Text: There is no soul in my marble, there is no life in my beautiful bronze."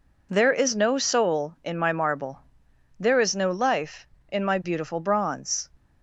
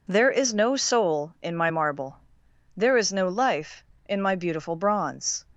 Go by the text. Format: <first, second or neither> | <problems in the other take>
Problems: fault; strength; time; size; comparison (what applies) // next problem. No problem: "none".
neither | none